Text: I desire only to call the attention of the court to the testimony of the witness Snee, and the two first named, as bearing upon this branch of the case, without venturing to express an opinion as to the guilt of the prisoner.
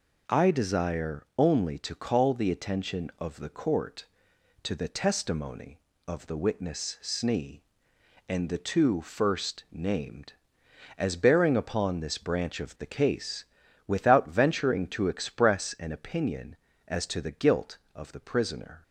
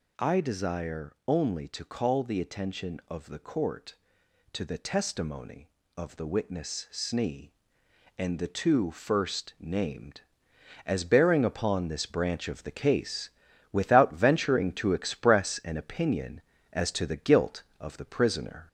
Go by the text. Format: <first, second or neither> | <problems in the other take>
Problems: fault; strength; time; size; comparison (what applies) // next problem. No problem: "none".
first | gets louder; slight; throughout; 2.5 dB